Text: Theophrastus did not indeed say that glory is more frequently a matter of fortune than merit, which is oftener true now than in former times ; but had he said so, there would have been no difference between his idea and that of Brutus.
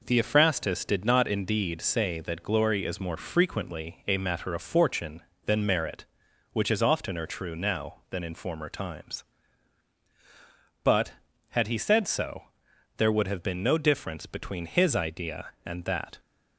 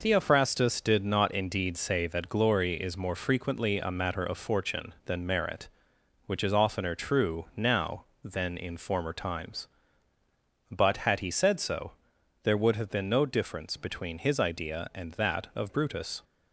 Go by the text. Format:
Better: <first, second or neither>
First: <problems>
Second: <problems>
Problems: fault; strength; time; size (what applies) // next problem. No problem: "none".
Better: second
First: stops before "of Brutus"; at 16.1 s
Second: none